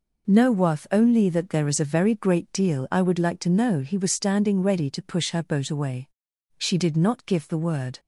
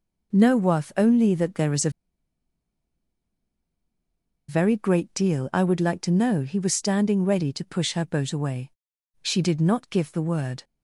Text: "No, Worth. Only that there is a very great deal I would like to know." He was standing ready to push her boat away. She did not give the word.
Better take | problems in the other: first | pauses between "a" and "very"; strong; at 1.8 s; 2.5 s long

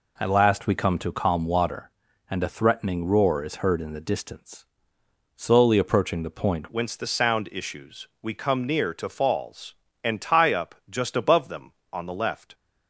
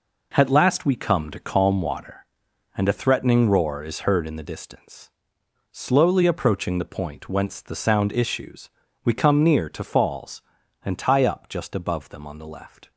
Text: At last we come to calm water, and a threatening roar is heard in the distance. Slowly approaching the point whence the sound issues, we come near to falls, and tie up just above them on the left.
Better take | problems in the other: second | changes voice at "whence"; from 6.6 s on; 5.9 s long

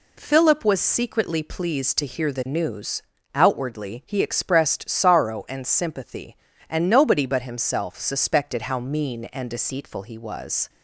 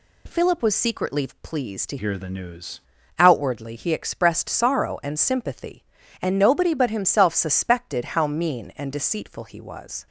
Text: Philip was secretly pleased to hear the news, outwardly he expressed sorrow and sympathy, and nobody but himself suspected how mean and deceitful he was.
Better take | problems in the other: first | changes voice from "hear" to "news"; from 1.9 to 2.7 s; 0.8 s long

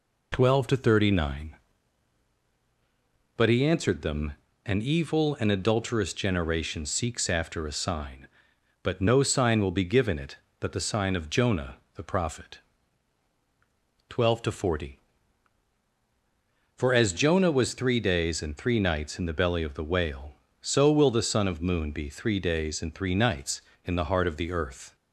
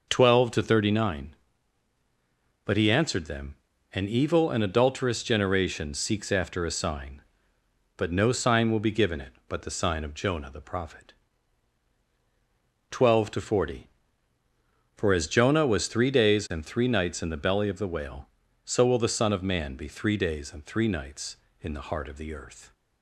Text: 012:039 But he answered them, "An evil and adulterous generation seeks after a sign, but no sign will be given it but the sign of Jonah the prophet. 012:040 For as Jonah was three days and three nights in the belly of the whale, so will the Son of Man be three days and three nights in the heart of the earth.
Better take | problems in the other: second | pauses between "Jonah" and "the"; slight; at 11.7 s; 0.20 s long // says "Moon" for "Man"; at 21.6 s

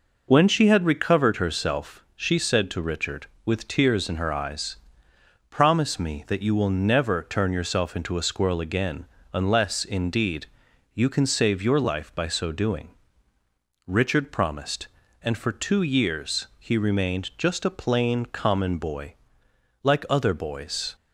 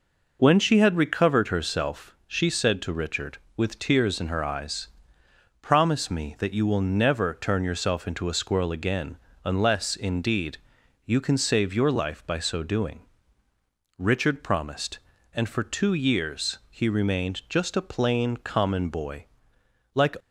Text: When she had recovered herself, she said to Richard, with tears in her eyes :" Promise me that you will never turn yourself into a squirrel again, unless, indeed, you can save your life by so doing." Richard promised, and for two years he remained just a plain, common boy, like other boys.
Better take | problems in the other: first | stops before "other boys"; at 20.2 s

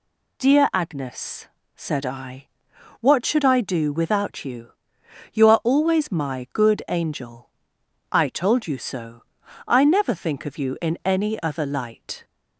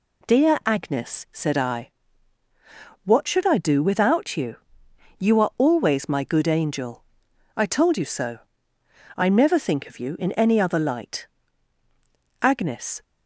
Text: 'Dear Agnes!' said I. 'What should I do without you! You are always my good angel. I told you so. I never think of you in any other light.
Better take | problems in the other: first | goes on to say "Agnes"; noticeable; from 12.3 s on; 0.62 s long

